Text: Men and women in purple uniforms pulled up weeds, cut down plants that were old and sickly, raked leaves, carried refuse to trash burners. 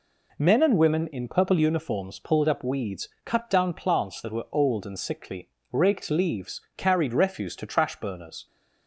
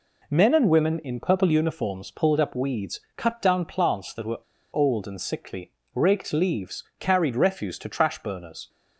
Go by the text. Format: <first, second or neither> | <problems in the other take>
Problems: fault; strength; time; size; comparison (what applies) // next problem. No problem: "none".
first | pauses between "were" and "old"; slight; at 4.3 s; 0.33 s long